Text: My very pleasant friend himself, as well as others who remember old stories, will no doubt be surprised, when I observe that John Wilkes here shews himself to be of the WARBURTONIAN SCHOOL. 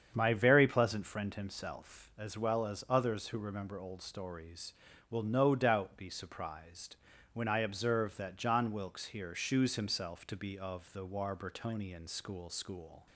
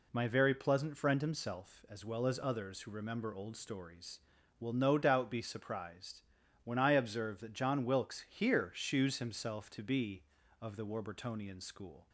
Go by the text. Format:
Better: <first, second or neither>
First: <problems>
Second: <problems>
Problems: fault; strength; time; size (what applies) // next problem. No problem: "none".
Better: second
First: starts louder than the rest; strong; until 1.1 s; 7.5 dB // says "SCHOOL" twice; at 12.4 s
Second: none